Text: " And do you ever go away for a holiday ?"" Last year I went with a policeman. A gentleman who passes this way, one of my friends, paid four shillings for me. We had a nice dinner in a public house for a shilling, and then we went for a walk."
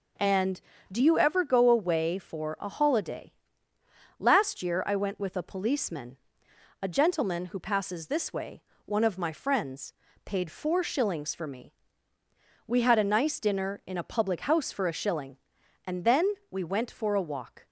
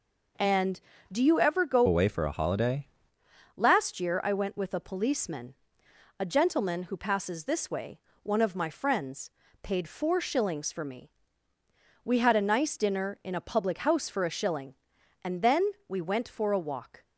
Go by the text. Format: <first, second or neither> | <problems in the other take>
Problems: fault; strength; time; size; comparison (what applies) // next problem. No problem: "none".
first | changes voice from "away" to "holiday"; from 1.8 to 2.8 s; 1.0 s long // pauses between "then" and "we"; slight; at 15.6 s; 0.16 s long; slight in the first